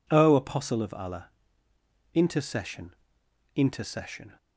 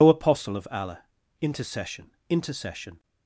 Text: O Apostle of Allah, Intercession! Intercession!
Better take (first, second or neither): first